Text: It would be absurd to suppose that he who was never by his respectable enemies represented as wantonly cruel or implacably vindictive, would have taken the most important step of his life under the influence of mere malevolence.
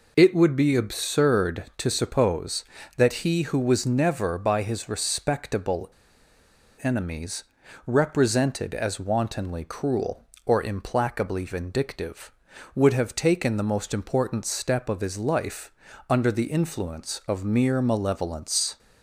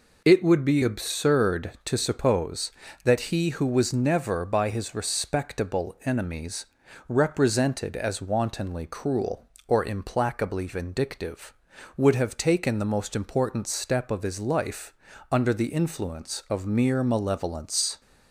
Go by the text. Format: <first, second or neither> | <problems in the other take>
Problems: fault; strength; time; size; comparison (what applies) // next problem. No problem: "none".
second | pauses between "respectable" and "enemies"; noticeable; at 5.9 s; 0.92 s long // pauses between "enemies" and "represented"; at 7.4 s; 0.42 s long; also in the second // pauses between "life" and "under"; at 15.7 s; 0.38 s long; also in the second